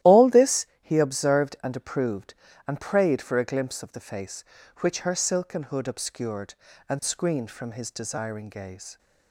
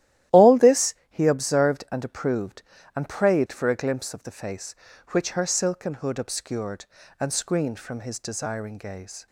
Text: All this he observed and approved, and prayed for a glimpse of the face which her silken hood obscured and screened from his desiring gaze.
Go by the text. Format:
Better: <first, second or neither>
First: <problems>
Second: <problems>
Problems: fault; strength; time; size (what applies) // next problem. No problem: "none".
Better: neither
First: starts louder than the rest; strong; until 1.2 s; 13.5 dB // pauses between "this" and "he"; slight; at 0.6 s; 0.16 s long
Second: starts louder than the rest; strong; until 1.4 s; 13.5 dB // pauses between "this" and "he"; slight; at 0.9 s; 0.16 s long